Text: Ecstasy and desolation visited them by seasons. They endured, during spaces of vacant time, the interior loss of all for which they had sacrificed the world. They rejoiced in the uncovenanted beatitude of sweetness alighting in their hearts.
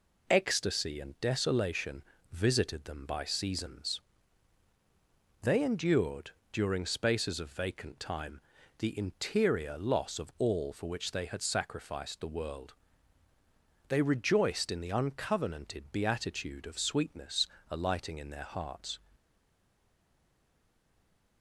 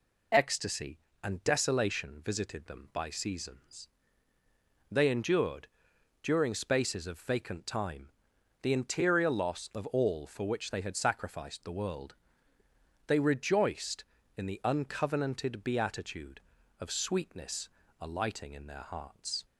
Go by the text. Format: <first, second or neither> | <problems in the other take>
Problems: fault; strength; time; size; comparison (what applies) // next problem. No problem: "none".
second | pauses between "desolation" and "visited"; slight; at 2.0 s; 0.30 s long // pauses between "sweetness" and "alighting"; slight; at 17.4 s; 0.24 s long; slight in the second // stays silent after the last word; from 19.1 s on; 2.3 s long